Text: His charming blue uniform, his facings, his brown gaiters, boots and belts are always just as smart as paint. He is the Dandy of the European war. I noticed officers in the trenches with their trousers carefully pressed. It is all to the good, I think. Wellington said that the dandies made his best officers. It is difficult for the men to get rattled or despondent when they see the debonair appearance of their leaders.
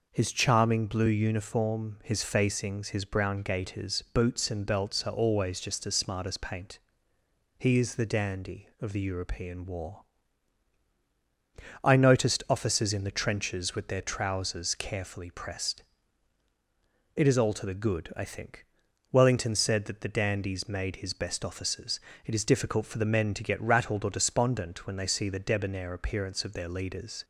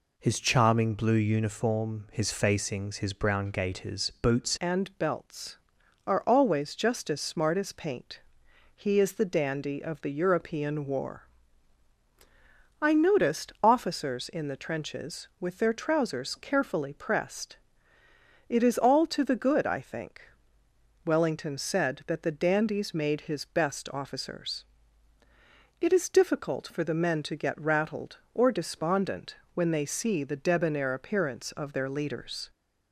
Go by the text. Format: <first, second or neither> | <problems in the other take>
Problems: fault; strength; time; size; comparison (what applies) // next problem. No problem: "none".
first | changes voice at "and"; from 4.5 s on; 27.9 s long // pauses between "despondent" and "when"; slight; at 29.3 s; 0.18 s long